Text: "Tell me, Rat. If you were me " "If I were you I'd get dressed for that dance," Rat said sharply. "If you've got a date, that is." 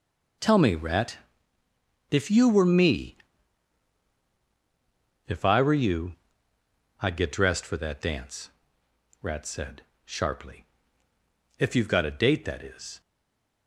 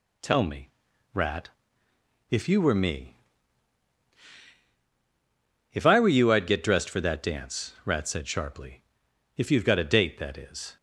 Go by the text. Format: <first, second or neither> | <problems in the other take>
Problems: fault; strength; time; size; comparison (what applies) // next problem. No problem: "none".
second | pauses between "you" and "I'd"; noticeable; at 6.1 s; 0.86 s long // pauses between "said" and "sharply"; slight; at 9.8 s; 0.22 s long // stays silent after the last word; slight; from 13.0 s on; 0.6 s long